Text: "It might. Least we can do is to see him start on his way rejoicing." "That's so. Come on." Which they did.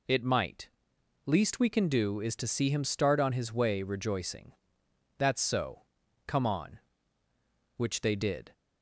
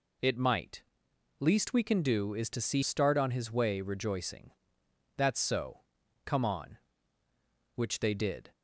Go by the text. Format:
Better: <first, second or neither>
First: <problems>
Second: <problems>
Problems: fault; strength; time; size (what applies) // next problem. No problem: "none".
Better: first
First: none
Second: skips "him"; at 2.8 s